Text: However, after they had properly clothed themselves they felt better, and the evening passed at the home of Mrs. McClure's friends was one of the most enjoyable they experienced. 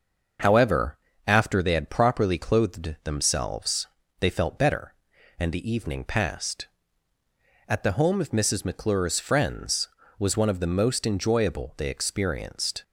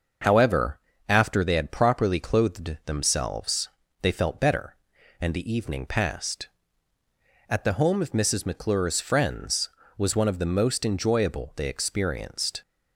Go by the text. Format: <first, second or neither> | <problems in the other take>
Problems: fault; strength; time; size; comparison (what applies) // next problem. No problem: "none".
neither | starts louder than the rest; the same in both // pauses between "themselves" and "they"; slight; the same in both